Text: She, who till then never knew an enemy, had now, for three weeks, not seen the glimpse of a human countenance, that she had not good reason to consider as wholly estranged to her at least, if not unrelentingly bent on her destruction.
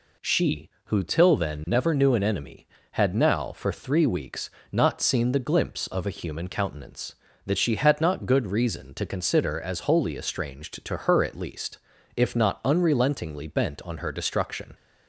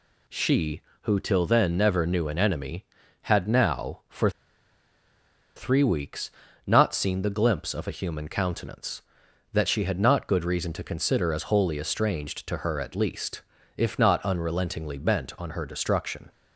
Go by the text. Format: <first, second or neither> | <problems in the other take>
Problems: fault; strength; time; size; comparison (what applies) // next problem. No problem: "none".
first | pauses between "for" and "three"; strong; at 4.2 s; 1.2 s long